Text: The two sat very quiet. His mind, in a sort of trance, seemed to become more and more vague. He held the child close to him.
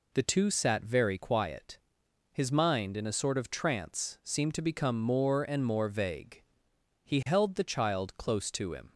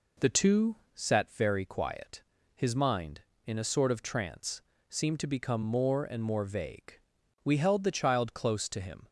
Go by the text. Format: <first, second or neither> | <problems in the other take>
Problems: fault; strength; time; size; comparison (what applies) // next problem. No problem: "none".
first | pauses between "two" and "sat"; slight; at 0.7 s; 0.22 s long // says "We" for "He"; at 7.4 s